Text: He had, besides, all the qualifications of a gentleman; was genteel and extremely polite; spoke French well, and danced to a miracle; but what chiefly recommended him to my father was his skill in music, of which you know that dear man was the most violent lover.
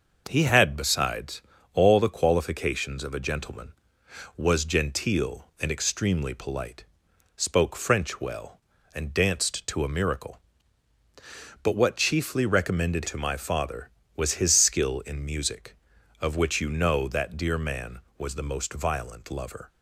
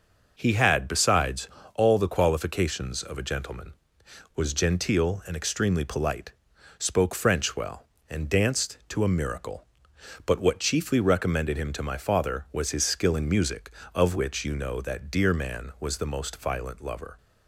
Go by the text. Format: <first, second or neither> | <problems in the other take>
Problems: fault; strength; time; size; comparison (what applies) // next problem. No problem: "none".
second | skips "him"; at 13.0 s